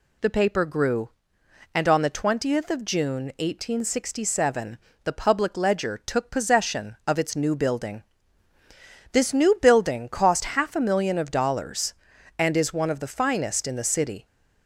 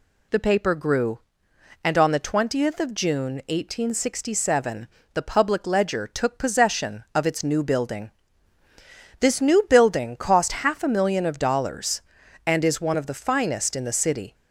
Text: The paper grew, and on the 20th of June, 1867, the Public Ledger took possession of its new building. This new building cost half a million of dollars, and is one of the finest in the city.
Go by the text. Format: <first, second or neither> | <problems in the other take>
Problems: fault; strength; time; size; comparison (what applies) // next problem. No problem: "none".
neither | none